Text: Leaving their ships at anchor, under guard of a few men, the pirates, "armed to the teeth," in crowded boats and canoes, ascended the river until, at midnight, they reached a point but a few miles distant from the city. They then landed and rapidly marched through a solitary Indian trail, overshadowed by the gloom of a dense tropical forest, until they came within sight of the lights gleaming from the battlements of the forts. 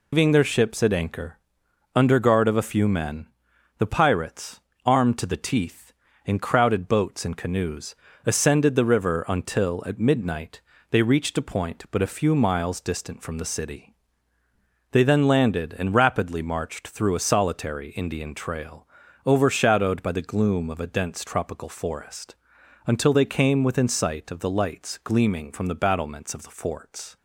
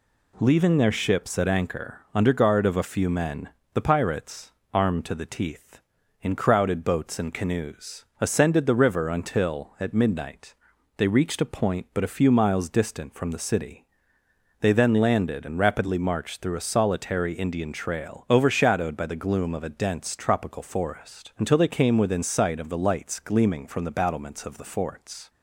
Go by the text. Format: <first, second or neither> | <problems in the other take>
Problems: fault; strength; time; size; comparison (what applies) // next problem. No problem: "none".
second | loses the start of "Leaving"; at 0.1 s; 160 ms